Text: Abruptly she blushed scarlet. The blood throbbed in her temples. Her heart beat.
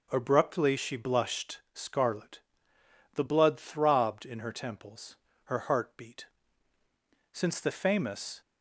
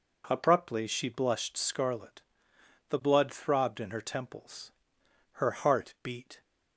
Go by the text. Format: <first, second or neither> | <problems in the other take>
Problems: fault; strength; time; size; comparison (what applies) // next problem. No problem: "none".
second | pauses between "blushed" and "scarlet"; slight; at 1.5 s; 0.16 s long // goes on to say "Since the famous"; noticeable; from 7.3 s on; 1.0 s long